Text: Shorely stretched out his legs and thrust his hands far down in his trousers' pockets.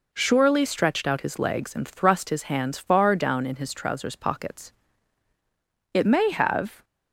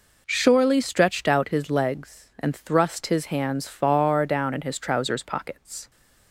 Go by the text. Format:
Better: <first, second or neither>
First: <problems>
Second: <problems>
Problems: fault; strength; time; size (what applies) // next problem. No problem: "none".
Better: second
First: goes on to say "It may have"; noticeable; from 5.9 s on; 0.90 s long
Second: none